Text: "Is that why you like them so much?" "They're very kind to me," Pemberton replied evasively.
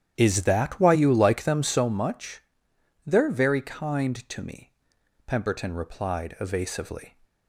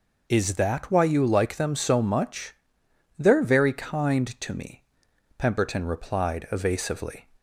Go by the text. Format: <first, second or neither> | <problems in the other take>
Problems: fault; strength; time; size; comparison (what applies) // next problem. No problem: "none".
second | starts louder than the rest; strong; until 1.8 s; 10 dB